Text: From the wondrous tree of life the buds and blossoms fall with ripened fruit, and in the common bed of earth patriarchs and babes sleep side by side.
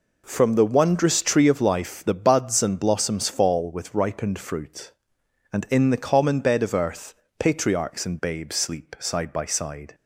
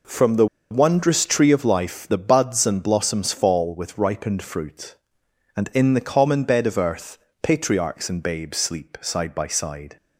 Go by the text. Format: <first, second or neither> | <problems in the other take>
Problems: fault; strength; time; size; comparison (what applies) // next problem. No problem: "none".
first | pauses between "the" and "wondrous"; slight; at 0.4 s; 0.25 s long // pauses between "earth" and "patriarchs"; slight; at 7.1 s; 0.24 s long; slight in the first